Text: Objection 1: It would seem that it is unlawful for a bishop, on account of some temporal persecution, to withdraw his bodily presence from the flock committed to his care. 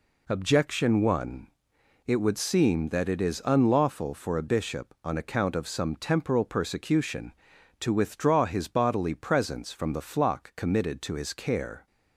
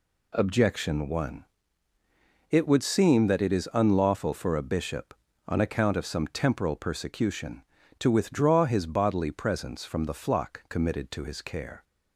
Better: neither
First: none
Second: none

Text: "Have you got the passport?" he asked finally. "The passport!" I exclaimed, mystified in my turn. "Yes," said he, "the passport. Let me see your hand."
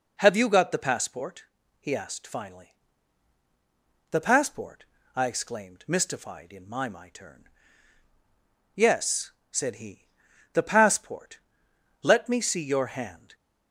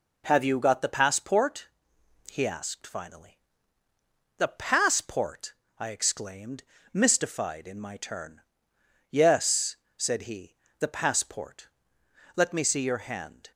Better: second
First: says "my" twice; at 6.8 s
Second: none

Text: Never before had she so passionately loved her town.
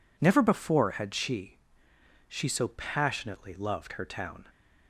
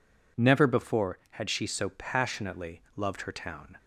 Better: second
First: says "she" twice; at 2.2 s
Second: none

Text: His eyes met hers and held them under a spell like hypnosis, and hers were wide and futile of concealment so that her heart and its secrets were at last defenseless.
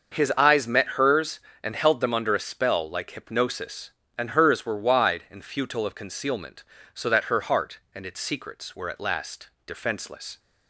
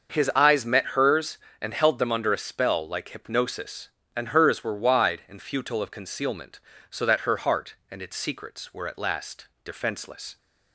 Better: neither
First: starts louder than the rest; until 1.1 s; 6.5 dB // pauses between "last" and "defenseless"; slight; at 9.5 s; 0.16 s long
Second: starts louder than the rest; until 1.1 s; 6.5 dB // pauses between "last" and "defenseless"; slight; at 9.4 s; 0.16 s long

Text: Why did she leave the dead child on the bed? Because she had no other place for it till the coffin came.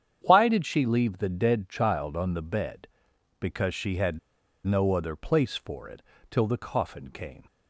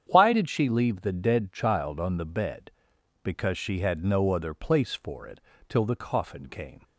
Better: second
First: starts louder than the rest; strong; until 1.2 s; 8.5 dB // pauses between "had" and "no"; noticeable; at 4.1 s; 0.47 s long // pauses between "it" and "till"; slight; at 6.0 s; 0.28 s long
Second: starts louder than the rest; strong; until 1.0 s; 8.5 dB // pauses between "it" and "till"; slight; at 5.3 s; 0.28 s long

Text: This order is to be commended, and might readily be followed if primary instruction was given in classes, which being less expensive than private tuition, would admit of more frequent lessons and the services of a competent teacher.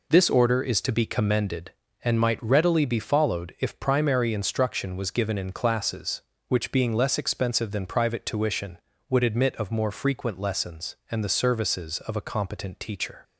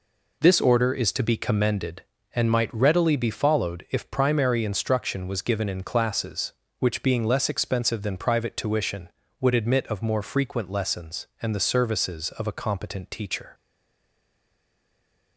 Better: first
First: none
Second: stays silent after the last word; noticeable; from 13.5 s on; 1.8 s long

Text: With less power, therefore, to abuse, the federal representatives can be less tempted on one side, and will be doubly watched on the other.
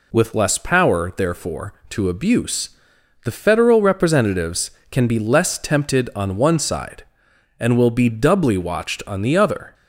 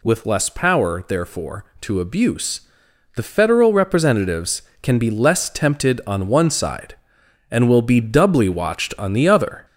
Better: first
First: none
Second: gets louder; throughout; 3.5 dB

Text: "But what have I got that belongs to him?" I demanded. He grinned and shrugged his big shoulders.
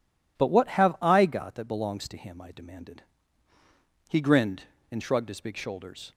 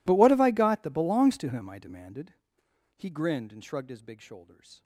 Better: first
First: none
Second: gets quieter; strong; throughout; 27.5 dB

